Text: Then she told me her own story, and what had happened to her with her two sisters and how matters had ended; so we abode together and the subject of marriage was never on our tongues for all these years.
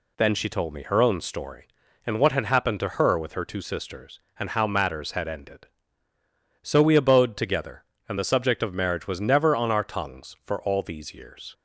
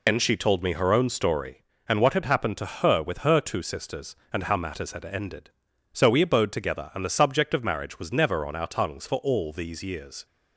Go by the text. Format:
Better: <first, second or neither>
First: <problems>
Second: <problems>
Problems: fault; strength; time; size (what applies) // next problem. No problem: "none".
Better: first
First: none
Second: loses the start of "Then"; at 0.0 s; 90 ms